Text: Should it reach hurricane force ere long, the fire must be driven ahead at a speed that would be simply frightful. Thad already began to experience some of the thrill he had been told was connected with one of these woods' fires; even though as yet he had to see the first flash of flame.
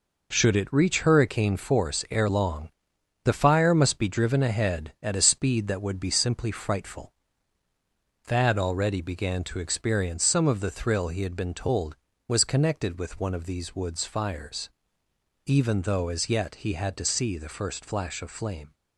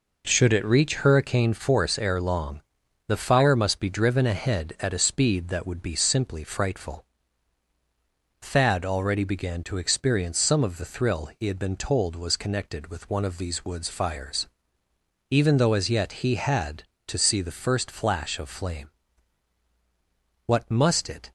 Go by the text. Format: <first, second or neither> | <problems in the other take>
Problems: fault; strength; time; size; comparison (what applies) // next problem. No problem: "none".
first | goes on to say "What must it"; noticeable; from 20.4 s on; 0.86 s long